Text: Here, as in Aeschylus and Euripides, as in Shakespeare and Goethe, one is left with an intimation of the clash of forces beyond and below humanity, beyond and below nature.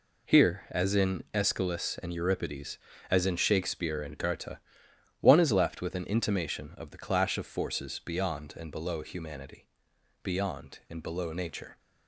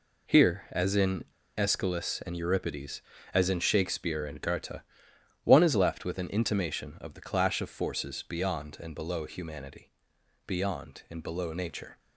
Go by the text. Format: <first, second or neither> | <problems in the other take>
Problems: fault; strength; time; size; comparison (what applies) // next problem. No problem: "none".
first | pauses between "in" and "Aeschylus"; at 1.2 s; 0.36 s long